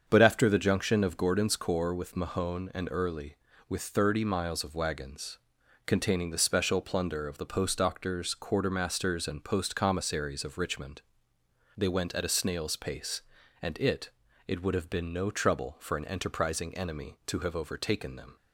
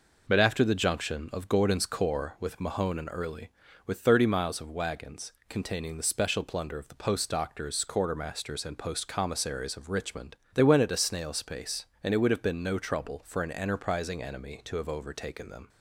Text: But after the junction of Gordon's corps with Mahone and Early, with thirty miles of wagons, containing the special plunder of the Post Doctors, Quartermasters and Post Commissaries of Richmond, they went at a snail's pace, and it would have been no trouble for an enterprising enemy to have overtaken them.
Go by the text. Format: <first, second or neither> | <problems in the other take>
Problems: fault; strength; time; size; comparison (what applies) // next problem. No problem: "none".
second | starts louder than the rest; until 1.0 s; 7 dB // says "it" twice; at 14.4 s